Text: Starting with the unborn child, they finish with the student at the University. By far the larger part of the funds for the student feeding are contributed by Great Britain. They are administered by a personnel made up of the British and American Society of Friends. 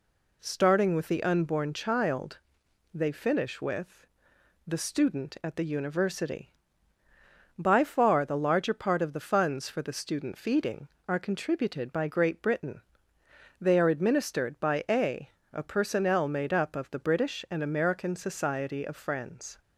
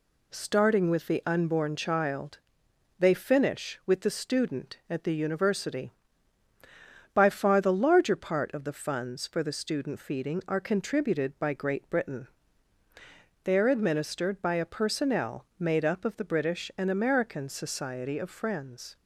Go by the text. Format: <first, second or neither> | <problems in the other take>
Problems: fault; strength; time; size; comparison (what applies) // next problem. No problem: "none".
second | pauses between "with" and "the"; noticeable; at 4.0 s; 0.60 s long // says "a" twice; at 15.5 s